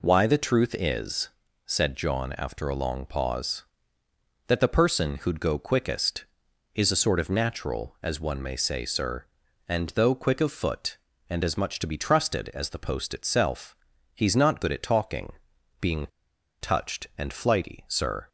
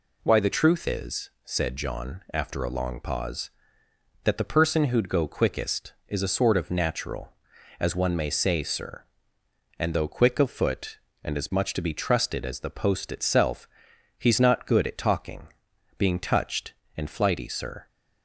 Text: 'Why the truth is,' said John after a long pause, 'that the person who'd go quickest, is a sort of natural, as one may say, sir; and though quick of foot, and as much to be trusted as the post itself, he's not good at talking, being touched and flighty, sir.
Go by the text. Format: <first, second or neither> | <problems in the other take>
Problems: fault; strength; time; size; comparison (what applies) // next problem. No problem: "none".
second | pauses between "being" and "touched"; noticeable; at 16.0 s; 0.54 s long